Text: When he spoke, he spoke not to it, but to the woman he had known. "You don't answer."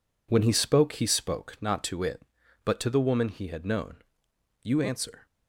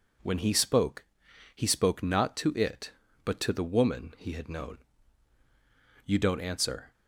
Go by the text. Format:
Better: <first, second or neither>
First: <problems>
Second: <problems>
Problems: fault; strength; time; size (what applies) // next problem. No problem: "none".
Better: second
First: skips "don't"; at 4.7 s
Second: none